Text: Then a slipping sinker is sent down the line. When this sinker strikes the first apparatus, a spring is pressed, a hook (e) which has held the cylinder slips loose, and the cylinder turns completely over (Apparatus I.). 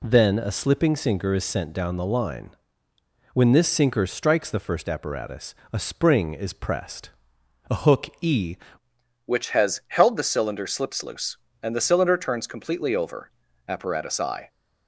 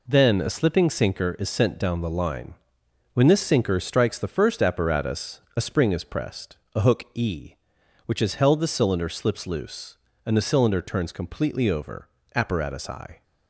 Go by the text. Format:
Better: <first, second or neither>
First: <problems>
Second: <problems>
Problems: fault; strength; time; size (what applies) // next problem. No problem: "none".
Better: second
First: changes voice at "which"; from 9.2 s on; 5.2 s long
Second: none